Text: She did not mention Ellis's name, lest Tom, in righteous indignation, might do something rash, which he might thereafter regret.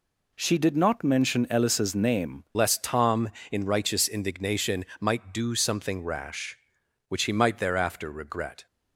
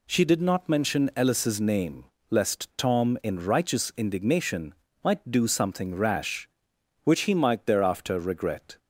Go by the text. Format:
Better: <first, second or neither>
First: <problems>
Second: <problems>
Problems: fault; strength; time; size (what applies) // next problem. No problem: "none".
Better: second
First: changes voice at "lest"; from 2.5 s on; 6.1 s long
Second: none